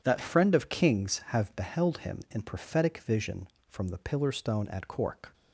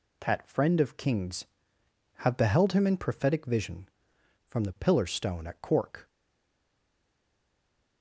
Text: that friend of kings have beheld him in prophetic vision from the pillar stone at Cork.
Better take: first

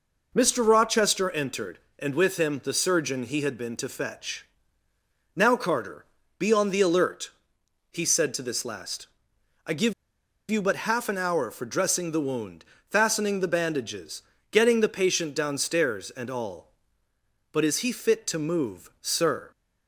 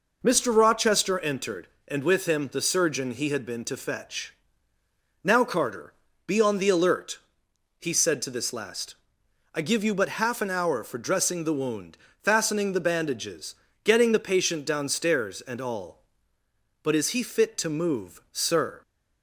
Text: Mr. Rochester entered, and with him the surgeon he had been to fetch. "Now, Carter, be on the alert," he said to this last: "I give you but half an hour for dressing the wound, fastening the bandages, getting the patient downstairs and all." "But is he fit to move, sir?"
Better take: second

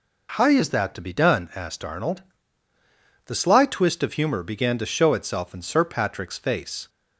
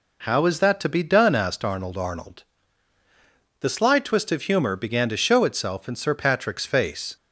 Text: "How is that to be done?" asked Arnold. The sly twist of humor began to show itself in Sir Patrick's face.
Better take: first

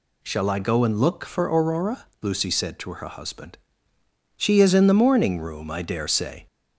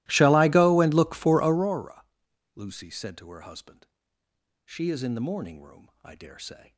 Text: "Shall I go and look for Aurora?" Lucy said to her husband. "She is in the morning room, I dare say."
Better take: first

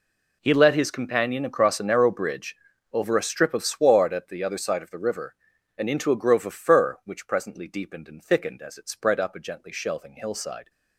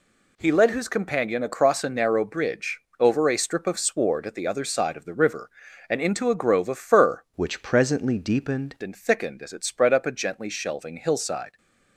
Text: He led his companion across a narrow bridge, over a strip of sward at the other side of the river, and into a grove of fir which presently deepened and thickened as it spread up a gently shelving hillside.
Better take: first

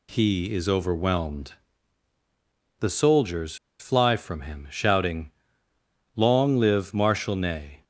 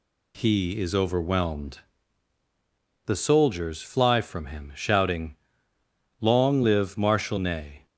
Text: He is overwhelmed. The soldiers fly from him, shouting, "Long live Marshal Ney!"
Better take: second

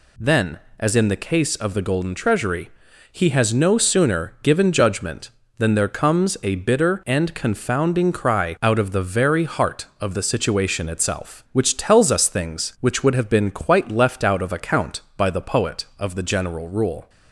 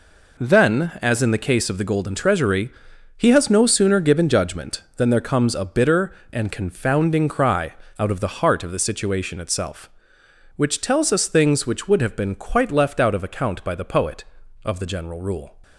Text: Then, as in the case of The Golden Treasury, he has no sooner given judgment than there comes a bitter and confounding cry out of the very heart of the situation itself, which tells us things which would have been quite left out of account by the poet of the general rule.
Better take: first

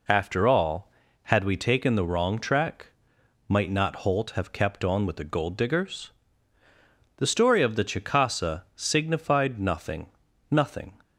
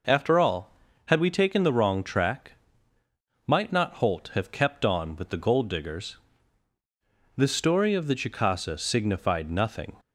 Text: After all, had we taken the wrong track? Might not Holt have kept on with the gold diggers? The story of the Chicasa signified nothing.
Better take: second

